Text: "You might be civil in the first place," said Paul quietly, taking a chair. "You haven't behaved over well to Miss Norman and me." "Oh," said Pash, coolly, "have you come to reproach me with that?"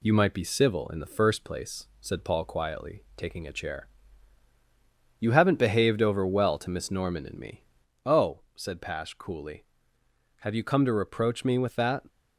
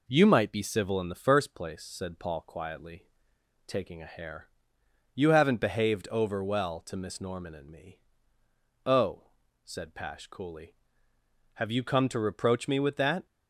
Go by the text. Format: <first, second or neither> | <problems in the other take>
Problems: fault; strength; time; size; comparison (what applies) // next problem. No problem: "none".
first | says "hair" for "chair"; at 4.1 s